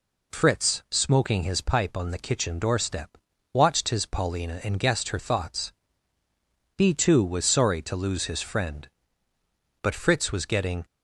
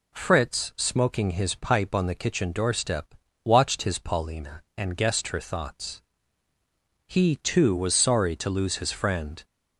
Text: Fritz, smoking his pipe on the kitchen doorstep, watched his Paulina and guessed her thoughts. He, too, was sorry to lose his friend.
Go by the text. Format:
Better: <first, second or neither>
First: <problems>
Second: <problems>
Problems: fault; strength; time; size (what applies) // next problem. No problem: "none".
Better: second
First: goes on to say "But Fritz was getting"; noticeable; from 9.8 s on; 1.0 s long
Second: none